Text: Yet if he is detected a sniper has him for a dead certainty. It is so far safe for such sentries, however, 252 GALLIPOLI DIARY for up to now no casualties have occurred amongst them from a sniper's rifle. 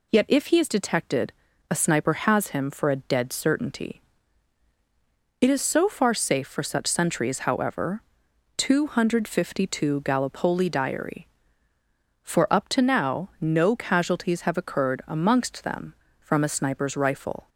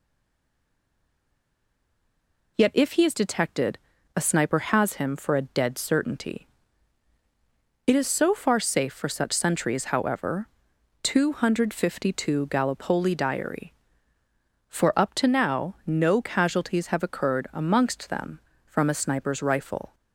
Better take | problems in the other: first | stays silent before the first word; strong; until 2.5 s; 2.5 s long // pauses between "detected" and "a"; at 3.7 s; 0.38 s long; also in the first

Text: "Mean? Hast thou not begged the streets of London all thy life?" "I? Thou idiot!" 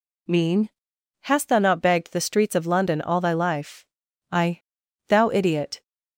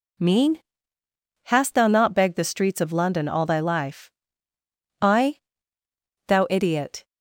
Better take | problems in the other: neither | none

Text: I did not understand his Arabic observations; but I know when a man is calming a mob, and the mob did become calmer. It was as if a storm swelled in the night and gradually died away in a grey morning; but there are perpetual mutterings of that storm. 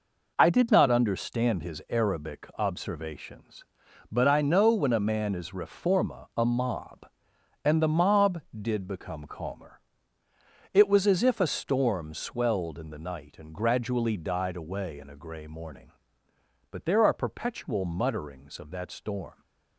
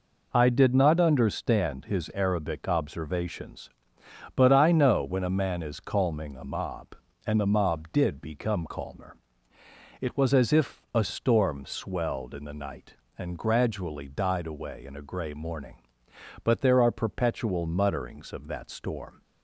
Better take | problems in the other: second | says "reforma" for "calming"; at 5.5 s

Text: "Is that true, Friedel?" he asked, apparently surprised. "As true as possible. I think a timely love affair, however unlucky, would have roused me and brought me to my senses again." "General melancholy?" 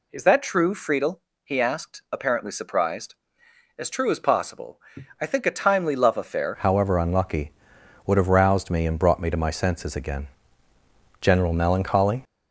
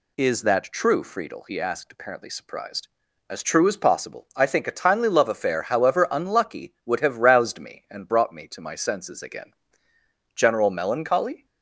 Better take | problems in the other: second | changes voice at "however"; from 6.5 s on; 5.7 s long

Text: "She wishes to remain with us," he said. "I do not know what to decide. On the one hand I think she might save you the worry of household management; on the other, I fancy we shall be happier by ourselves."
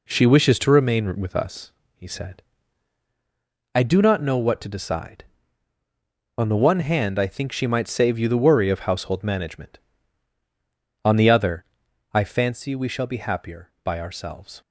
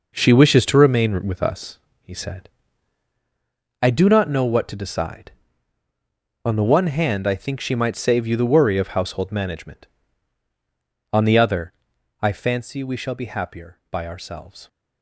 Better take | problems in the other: first | gets quieter; strong; throughout; 9.5 dB

